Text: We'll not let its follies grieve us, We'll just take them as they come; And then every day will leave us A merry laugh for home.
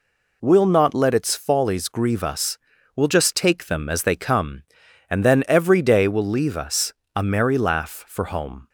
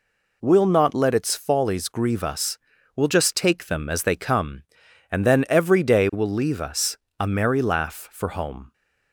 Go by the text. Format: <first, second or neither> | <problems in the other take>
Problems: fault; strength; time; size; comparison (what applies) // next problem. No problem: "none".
neither | pauses between "us" and "A"; slight; the same in both